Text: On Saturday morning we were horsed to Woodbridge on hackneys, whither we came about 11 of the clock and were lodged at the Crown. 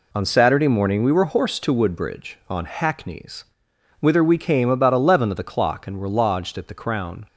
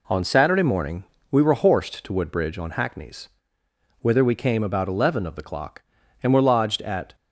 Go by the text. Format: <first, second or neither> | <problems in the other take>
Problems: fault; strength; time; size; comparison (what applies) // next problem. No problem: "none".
first | pauses between "morning" and "we"; slight; at 1.0 s; 0.28 s long // stops before "the Crown"; at 7.1 s